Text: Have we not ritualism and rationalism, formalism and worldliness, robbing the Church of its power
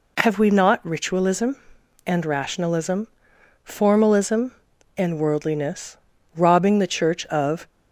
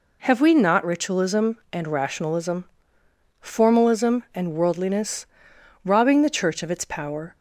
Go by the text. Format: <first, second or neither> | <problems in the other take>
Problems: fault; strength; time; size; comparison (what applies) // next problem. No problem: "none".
second | stops before "its power"; at 7.6 s